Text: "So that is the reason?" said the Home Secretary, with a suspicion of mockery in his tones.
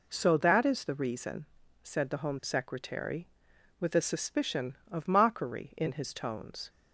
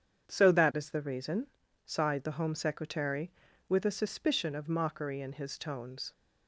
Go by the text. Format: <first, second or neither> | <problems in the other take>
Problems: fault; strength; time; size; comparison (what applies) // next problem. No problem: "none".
first | starts louder than the rest; strong; until 1.3 s; 8 dB // says "sighed" for "said"; at 1.8 s